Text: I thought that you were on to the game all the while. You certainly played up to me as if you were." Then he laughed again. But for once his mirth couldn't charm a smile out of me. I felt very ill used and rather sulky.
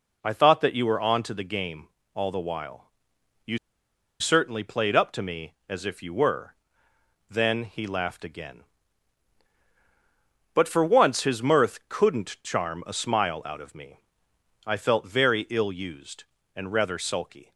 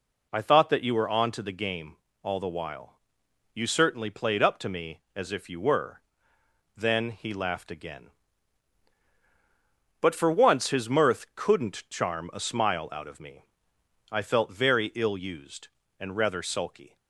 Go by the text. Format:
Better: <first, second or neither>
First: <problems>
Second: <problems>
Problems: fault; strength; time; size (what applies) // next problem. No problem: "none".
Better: second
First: pauses between "game" and "all"; slight; at 1.8 s; 0.26 s long // pauses between "You" and "certainly"; noticeable; at 3.5 s; 0.64 s long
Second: pauses between "game" and "all"; slight; at 1.9 s; 0.26 s long